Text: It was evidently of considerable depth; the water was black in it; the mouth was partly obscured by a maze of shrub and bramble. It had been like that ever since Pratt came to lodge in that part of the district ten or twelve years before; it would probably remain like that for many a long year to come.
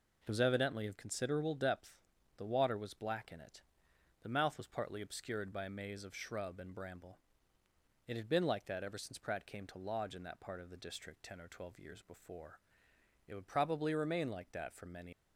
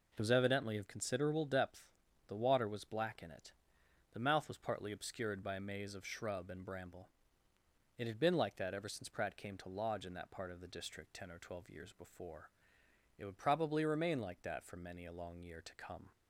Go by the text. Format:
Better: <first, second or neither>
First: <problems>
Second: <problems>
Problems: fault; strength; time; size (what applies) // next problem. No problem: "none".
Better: second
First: stops before "a long year to come"; at 15.1 s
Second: none